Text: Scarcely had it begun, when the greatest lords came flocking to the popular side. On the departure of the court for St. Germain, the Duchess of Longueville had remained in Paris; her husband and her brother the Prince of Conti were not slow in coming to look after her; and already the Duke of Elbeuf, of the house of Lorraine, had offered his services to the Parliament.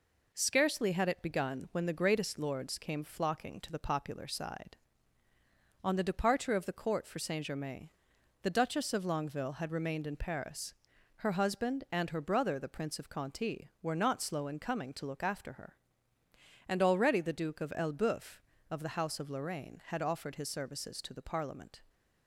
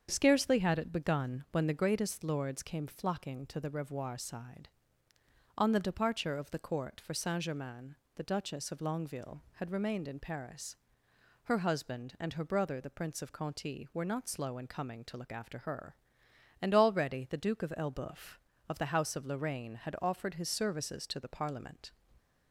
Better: first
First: none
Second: starts louder than the rest; strong; until 1.1 s; 7.5 dB // says "revoir" for "popular"; at 3.6 s

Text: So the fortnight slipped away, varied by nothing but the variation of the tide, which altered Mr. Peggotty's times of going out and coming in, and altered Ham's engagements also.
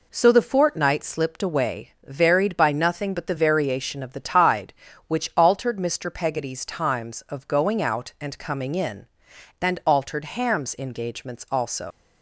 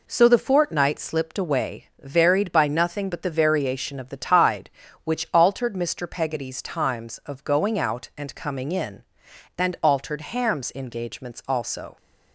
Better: second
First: leaves "also" unfinished; at 11.9 s; 95 ms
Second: none

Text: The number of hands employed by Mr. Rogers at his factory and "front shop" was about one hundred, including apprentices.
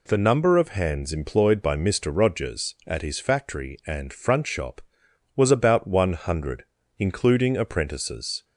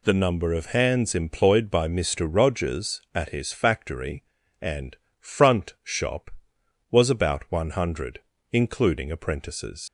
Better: first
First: none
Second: pauses between "and" and "front"; slight; at 4.9 s; 0.24 s long // leaves "apprentices" unfinished; at 9.8 s; 70 ms

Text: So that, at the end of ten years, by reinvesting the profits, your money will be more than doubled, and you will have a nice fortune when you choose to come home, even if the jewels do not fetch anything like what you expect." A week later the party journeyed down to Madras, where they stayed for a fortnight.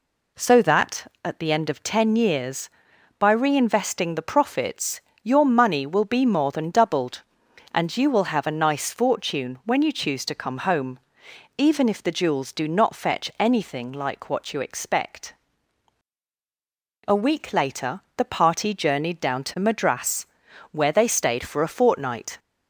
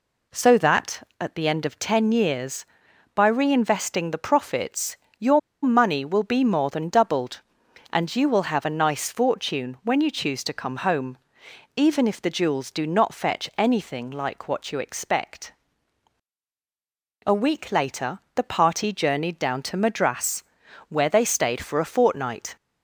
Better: first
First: pauses between "later" and "the"; slight; at 17.9 s; 0.16 s long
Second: pauses between "your" and "money"; slight; at 5.3 s; 0.24 s long // pauses between "later" and "the"; slight; at 18.1 s; 0.16 s long

